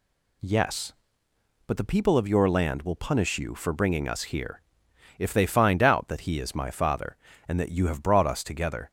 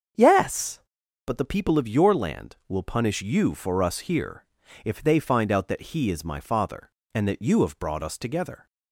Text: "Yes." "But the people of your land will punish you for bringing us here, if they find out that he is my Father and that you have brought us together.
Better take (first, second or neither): first